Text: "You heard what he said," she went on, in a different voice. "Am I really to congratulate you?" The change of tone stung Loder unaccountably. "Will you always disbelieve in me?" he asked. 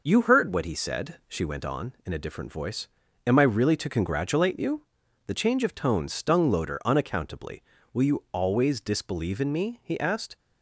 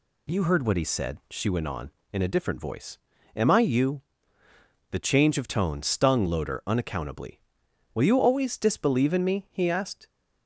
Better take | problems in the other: first | skips "really to congratulate"; at 3.6 s

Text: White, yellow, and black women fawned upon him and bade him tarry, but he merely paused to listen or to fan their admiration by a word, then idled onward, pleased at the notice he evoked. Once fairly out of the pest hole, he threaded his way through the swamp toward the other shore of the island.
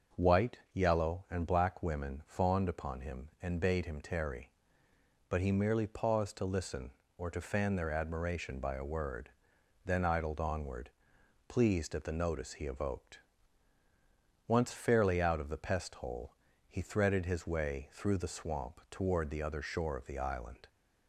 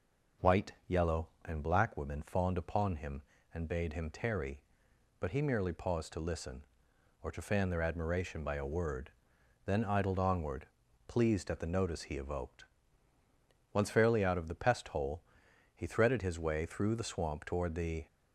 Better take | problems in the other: first | stops before "other shore of the island"; at 18.0 s

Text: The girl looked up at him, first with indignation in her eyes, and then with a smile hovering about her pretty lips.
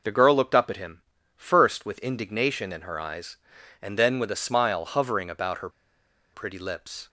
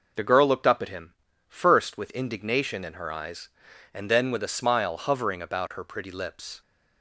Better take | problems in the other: second | pauses between "her" and "pretty"; noticeable; at 5.6 s; 0.65 s long

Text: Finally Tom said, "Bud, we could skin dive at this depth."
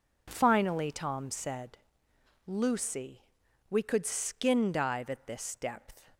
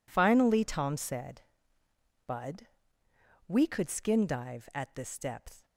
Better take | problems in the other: second | says "Lucy" for "Bud"; at 2.4 s

